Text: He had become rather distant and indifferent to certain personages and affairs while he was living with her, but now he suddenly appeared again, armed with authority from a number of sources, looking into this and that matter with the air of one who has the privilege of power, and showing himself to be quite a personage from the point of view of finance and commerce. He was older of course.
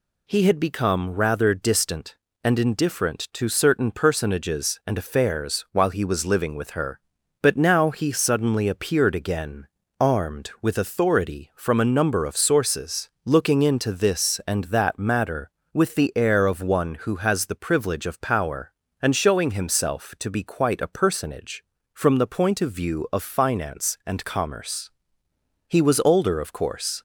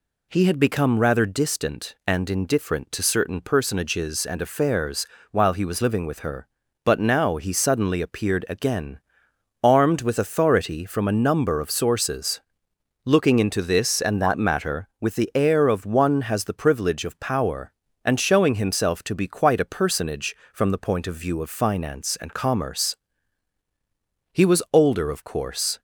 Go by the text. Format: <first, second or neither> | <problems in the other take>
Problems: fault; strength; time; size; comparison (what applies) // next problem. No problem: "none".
first | pauses between "affairs" and "while"; slight; at 5.0 s; 0.24 s long // skips "who"; at 16.2 s